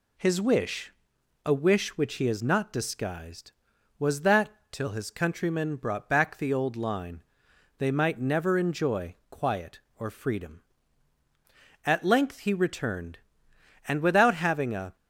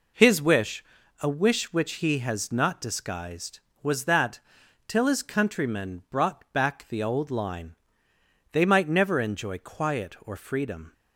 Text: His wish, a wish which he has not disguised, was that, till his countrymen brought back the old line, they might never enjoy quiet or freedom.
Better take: second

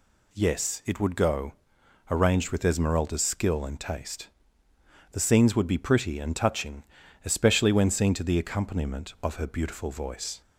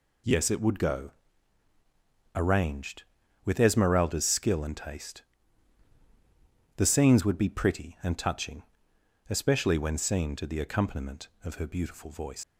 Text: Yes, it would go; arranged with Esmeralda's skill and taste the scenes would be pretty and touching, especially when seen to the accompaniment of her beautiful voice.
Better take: first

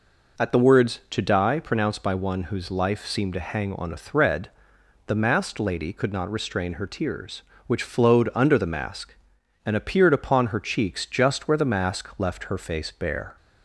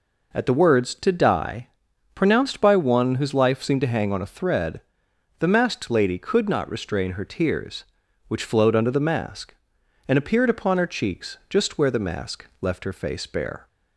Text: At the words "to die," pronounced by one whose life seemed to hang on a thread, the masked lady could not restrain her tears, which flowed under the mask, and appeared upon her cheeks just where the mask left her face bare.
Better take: neither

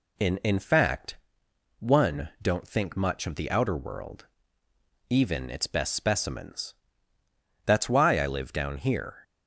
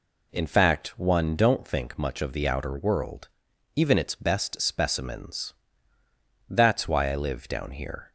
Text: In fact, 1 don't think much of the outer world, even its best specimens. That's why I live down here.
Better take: second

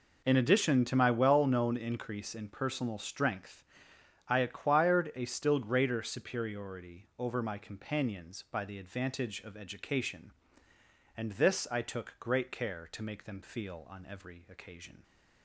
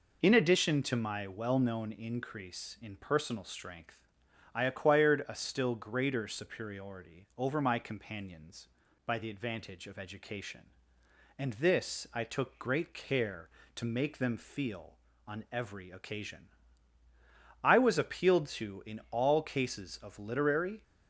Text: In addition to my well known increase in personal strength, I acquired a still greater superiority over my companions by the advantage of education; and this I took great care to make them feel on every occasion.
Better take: first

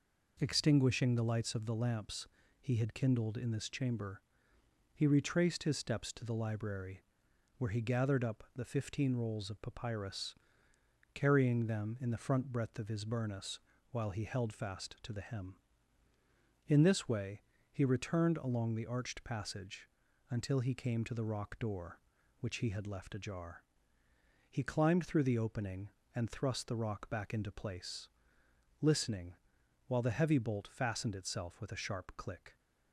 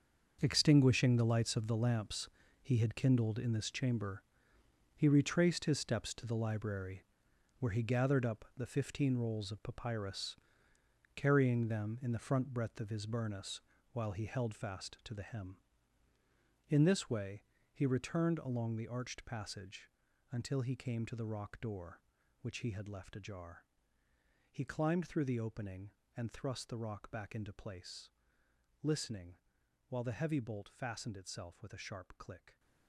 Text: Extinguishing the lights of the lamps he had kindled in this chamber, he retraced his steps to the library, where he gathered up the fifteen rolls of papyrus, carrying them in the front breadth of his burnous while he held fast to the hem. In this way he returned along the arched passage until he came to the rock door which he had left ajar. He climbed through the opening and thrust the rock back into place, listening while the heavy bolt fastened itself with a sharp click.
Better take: first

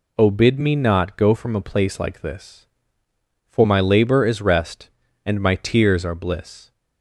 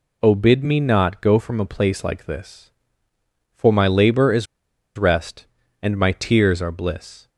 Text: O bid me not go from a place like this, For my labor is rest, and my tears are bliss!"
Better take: first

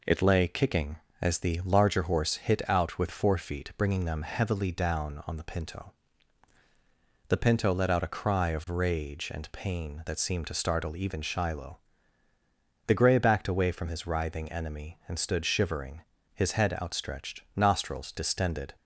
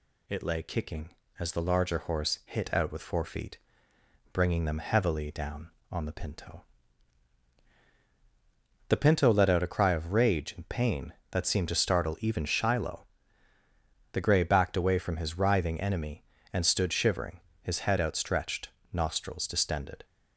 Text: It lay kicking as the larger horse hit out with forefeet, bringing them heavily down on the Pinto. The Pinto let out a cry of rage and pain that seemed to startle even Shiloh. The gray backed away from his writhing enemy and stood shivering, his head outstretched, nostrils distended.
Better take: neither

